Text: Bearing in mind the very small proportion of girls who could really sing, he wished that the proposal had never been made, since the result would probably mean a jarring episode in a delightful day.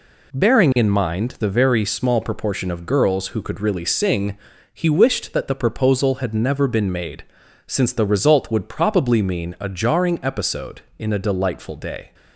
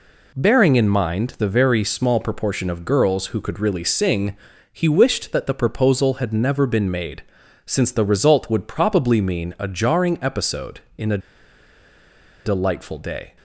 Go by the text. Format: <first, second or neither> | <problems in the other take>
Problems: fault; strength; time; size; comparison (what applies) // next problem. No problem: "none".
first | pauses between "a" and "delightful"; strong; at 11.1 s; 1.2 s long